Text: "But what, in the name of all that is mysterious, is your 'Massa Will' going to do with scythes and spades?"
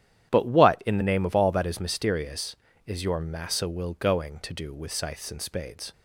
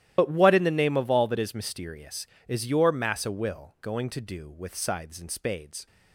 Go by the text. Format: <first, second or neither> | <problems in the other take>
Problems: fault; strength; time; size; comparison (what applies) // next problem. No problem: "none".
first | loses the start of "But"; at 0.1 s; 55 ms // starts louder than the rest; strong; until 1.1 s; 13 dB; strong in the first